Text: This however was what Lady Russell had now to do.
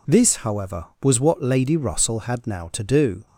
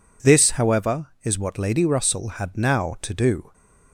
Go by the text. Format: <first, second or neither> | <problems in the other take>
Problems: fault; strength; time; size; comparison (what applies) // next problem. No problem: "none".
first | says "is" for "was"; at 1.2 s